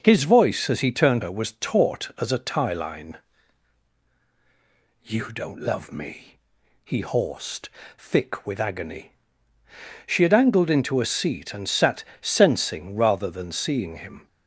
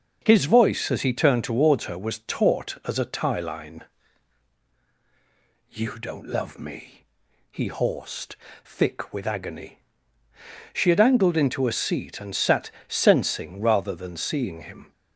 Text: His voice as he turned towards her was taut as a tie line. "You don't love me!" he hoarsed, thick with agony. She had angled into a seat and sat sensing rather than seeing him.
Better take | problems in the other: second | skips "towards"; at 1.2 s // pauses between "sat" and "sensing"; slight; at 12.0 s; 0.18 s long; slight in the second

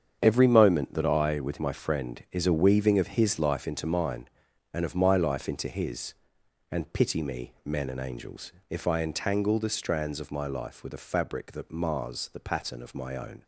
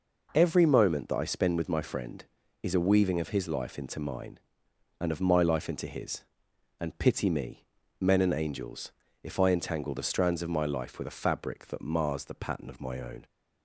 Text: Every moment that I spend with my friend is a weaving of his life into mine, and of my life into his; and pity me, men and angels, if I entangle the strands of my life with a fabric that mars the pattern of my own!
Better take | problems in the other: second | starts louder than the rest; strong; until 1.2 s; 7.5 dB // skips "spend"; at 1.3 s

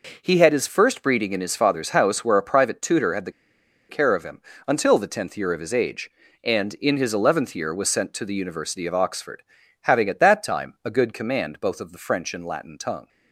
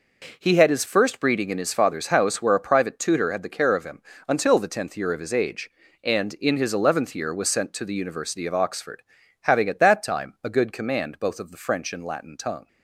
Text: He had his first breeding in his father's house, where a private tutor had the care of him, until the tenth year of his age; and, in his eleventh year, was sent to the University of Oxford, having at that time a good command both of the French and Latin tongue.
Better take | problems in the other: second | pauses between "the" and "care"; noticeable; at 3.3 s; 0.57 s long

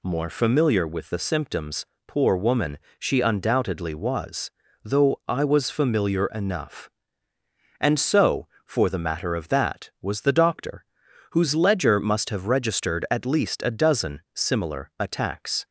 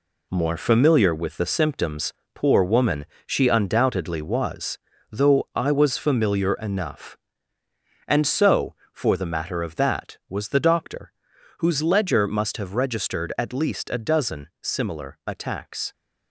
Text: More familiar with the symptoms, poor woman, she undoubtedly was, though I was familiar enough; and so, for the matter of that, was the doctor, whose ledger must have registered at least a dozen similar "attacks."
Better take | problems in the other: first | gets quieter; strong; throughout; 7.5 dB

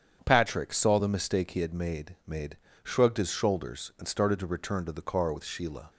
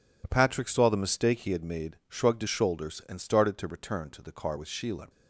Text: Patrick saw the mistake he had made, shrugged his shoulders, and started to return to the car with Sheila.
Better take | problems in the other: second | starts louder than the rest; strong; until 1.2 s; 8 dB // says "made" twice; at 2.2 s

